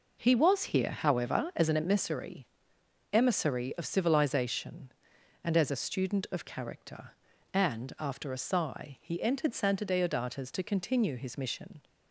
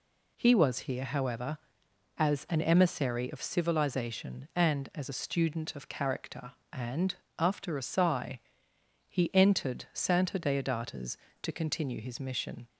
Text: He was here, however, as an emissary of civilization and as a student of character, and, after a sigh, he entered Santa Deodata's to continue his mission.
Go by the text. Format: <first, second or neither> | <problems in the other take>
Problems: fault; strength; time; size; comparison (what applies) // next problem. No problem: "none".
second | says "emissary" twice; at 3.1 s